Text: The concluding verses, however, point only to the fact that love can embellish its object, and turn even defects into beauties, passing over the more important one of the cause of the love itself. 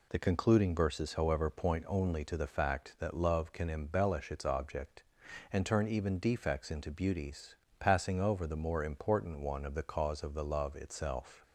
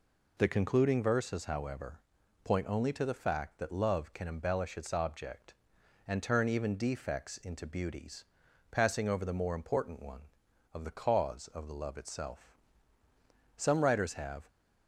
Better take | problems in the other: first | goes on to say "Some writers have"; noticeable; from 13.5 s on; 0.92 s long

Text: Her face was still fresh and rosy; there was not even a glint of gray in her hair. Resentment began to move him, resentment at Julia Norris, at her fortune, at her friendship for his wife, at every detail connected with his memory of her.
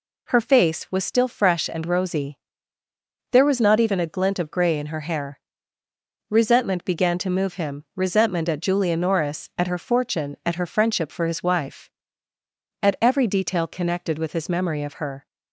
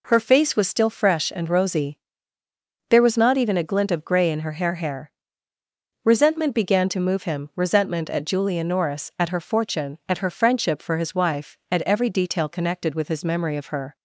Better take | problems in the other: first | says "hair" twice; at 4.7 s

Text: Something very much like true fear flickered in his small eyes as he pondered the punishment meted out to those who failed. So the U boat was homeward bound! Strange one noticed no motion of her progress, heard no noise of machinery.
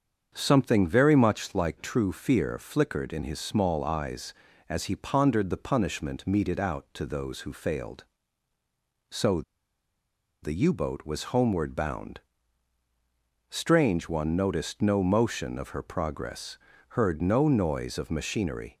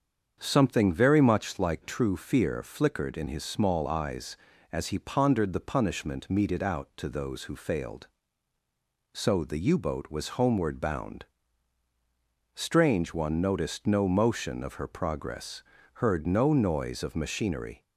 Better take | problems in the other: second | starts louder than the rest; strong; until 1.3 s; 7 dB; strong in the second // pauses between "So" and "the"; at 9.4 s; 1.0 s long

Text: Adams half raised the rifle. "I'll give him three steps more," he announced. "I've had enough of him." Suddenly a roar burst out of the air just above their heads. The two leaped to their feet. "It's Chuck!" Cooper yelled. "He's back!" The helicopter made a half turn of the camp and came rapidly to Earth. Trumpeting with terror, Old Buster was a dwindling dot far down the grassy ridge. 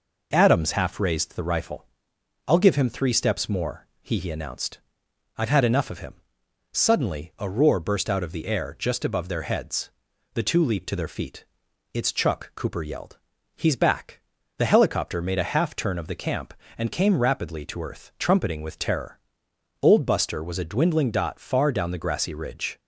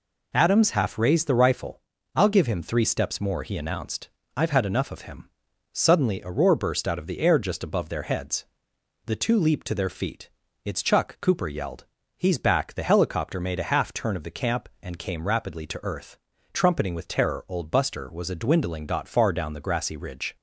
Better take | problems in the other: second | says "he" twice; at 4.1 s

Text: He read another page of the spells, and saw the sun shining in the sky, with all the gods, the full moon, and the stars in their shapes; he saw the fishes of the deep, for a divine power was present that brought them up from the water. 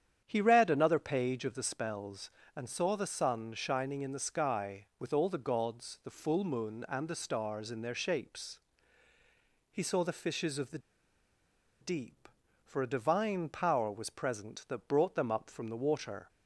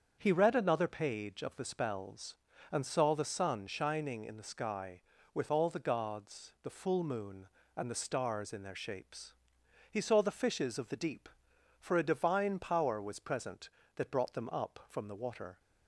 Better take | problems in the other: second | starts louder than the rest; strong; until 1.2 s; 9 dB; strong in the second // pauses between "the" and "deep"; at 10.7 s; 1.0 s long

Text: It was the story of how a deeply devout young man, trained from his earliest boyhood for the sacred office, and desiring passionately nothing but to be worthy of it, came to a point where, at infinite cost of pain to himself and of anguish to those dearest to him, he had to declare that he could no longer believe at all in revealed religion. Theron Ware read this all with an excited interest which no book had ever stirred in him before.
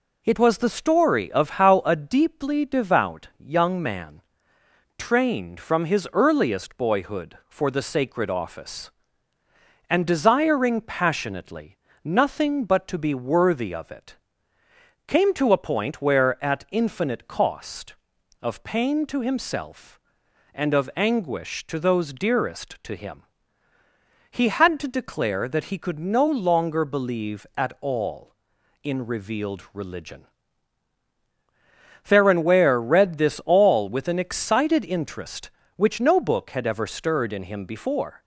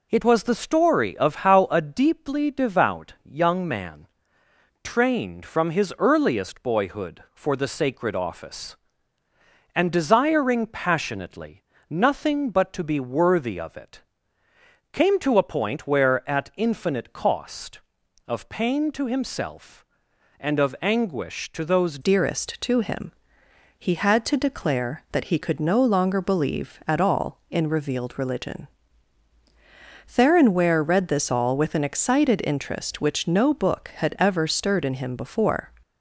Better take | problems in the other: first | pauses between "passionately" and "nothing"; slight; at 11.6 s; 0.30 s long; slight in the first // changes voice at "dearest"; from 22.0 s on; 13.7 s long

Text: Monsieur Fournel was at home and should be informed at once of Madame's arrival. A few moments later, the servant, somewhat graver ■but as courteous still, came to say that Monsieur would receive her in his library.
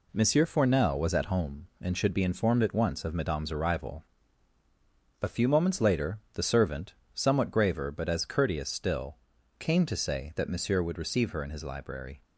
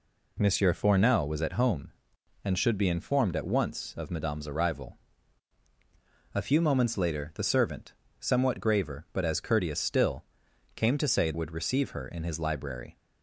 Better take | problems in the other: first | skips "that Monsieur"; at 11.3 s

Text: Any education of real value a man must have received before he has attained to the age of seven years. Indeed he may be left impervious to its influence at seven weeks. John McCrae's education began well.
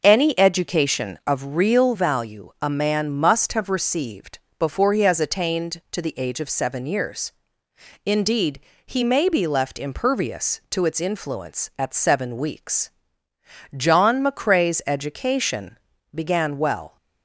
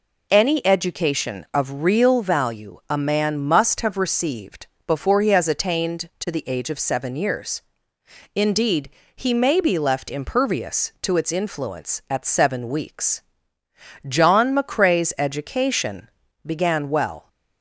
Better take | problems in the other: second | starts louder than the rest; noticeable; until 1.2 s; 5.5 dB // pauses between "received" and "before"; slight; at 4.3 s; 0.22 s long; slight in the second // pauses between "Indeed" and "he"; slight; at 8.6 s; 0.26 s long; slight in the second // pauses between "education" and "began"; slight; at 15.7 s; 0.34 s long; slight in the second

